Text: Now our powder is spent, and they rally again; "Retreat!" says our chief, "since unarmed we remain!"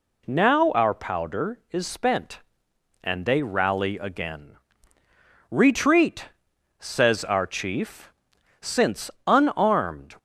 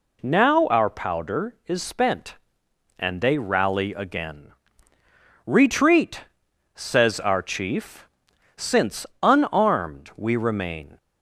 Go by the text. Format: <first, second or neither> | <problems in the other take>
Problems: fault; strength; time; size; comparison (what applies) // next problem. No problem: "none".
second | pauses between "since" and "unarmed"; slight; at 9.1 s; 0.16 s long; slight in the second // stops before "we remain"; at 10.1 s